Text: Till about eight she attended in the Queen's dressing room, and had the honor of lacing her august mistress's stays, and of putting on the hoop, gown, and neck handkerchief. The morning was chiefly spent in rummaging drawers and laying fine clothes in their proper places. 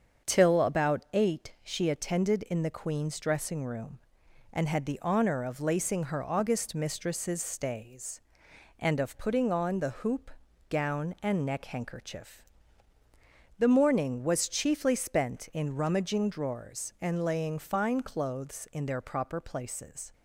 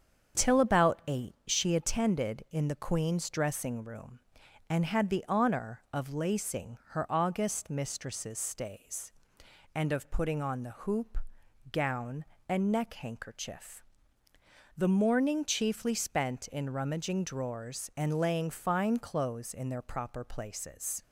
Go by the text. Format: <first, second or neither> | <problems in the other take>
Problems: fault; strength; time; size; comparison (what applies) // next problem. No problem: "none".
first | starts louder than the rest; strong; until 1.5 s; 7.5 dB; also in the first // skips "was"; at 15.4 s